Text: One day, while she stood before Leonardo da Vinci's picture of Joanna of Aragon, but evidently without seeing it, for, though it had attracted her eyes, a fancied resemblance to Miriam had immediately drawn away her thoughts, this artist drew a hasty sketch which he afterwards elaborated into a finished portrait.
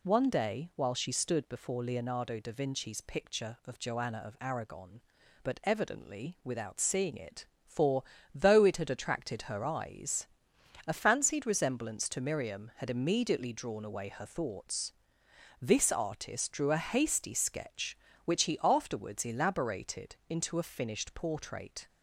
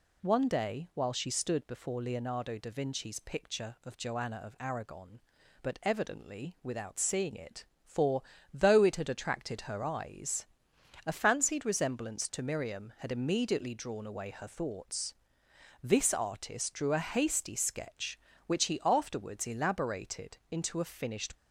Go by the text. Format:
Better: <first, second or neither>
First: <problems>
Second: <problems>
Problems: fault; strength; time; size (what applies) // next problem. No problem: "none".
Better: first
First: none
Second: stops before "portrait"; at 21.3 s